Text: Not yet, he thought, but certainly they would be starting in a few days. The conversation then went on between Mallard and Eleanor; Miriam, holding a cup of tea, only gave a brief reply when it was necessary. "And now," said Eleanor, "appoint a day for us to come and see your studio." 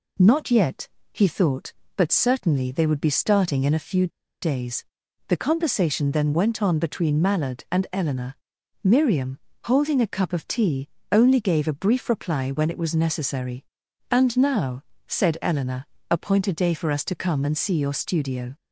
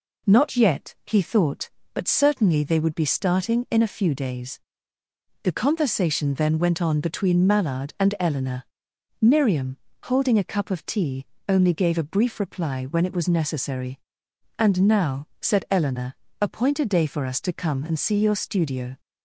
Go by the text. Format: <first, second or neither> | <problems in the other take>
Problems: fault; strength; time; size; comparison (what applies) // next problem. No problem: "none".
second | pauses between "few" and "days"; slight; at 4.0 s; 0.34 s long